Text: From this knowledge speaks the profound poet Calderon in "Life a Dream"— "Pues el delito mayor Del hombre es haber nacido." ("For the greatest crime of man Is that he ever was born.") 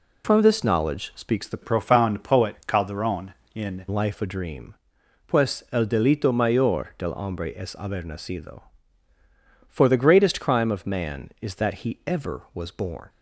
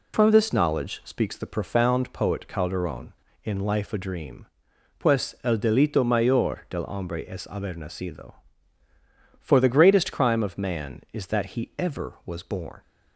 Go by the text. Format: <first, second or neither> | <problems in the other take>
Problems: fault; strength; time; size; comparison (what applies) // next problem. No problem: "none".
second | changes voice from "profound" to "in"; from 1.6 to 3.8 s; 2.2 s long